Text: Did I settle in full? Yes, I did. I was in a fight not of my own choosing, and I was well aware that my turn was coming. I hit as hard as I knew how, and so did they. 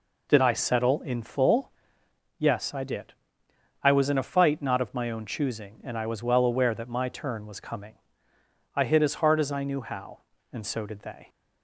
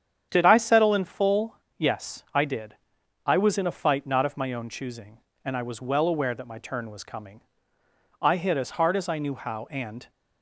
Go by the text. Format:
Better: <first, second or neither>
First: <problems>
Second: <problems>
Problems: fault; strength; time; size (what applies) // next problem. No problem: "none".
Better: first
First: none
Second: starts louder than the rest; strong; until 1.3 s; 8.5 dB // stops before "so did they"; at 10.0 s